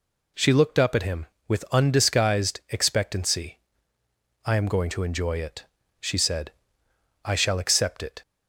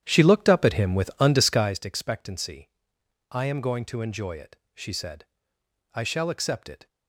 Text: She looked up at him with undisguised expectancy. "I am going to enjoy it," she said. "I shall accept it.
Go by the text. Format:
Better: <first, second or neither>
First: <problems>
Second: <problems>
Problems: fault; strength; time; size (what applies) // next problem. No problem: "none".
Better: first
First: none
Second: starts louder than the rest; strong; until 1.7 s; 10 dB